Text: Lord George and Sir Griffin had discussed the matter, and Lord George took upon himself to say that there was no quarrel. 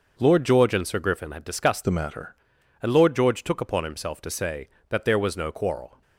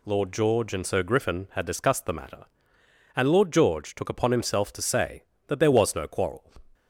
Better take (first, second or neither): second